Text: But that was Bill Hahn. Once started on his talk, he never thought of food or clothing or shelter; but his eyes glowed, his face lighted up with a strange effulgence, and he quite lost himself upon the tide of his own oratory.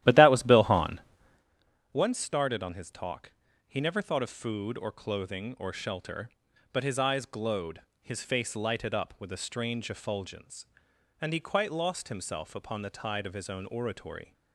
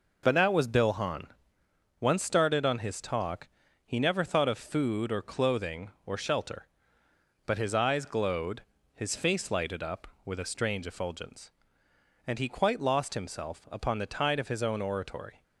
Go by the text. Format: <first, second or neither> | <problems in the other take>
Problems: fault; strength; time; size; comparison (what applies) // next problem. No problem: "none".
second | starts louder than the rest; strong; until 1.5 s; 13 dB